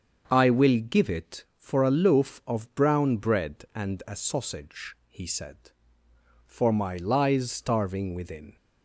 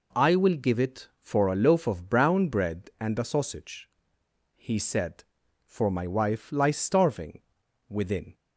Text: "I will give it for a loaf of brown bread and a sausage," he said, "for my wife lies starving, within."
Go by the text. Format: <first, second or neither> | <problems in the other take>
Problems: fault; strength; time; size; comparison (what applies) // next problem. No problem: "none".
second | starts louder than the rest; until 1.3 s; 7 dB // skips "wife"; at 6.9 s